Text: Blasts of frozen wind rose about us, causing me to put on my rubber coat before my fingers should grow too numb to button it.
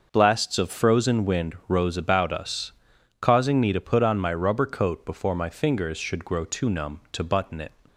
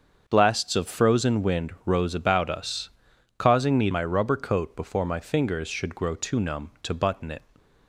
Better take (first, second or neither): first